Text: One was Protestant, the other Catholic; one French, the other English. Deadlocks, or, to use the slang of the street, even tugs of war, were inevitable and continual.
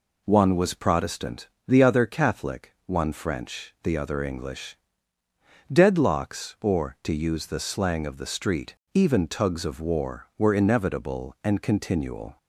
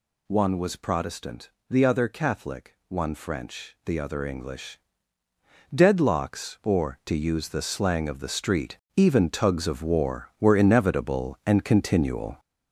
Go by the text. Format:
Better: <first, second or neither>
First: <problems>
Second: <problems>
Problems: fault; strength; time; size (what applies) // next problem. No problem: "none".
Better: first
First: none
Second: gets louder; throughout; 6.5 dB